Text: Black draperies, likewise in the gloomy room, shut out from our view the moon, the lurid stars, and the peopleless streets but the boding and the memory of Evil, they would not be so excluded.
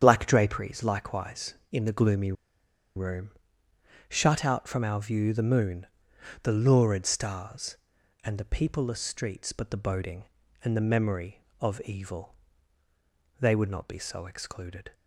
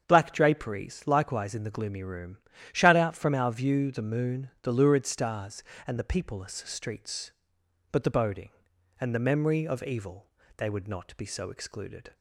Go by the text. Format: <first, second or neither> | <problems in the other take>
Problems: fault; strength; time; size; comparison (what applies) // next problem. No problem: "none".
second | starts louder than the rest; strong; until 1.0 s; 8.5 dB; strong in the second // pauses between "gloomy" and "room"; noticeable; at 2.3 s; 0.63 s long